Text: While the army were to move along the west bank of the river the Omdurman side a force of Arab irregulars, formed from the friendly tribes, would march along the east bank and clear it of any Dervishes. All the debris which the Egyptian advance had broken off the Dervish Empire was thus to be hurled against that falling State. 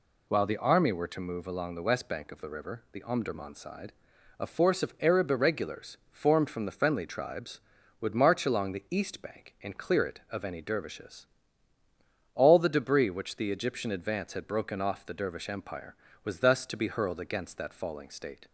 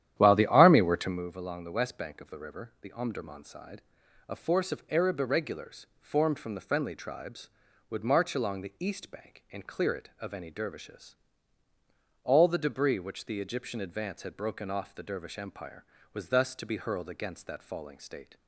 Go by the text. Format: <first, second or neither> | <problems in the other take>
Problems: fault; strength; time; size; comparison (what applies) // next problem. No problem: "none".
first | starts louder than the rest; strong; until 1.3 s; 11 dB // pauses between "side" and "a"; noticeable; at 3.8 s; 0.48 s long; noticeable in the first